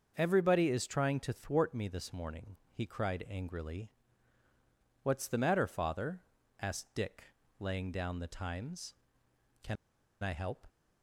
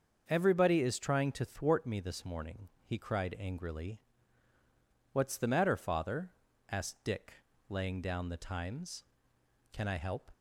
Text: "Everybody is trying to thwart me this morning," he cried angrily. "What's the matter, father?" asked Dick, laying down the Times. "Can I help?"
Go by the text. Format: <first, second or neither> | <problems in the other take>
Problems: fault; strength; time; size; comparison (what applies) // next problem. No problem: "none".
second | starts louder than the rest; until 1.1 s; 6.5 dB; also in the second // pauses between "Can" and "I"; at 9.7 s; 0.45 s long